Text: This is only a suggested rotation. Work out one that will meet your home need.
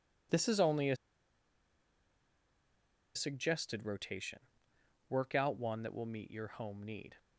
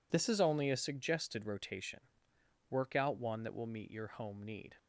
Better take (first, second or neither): second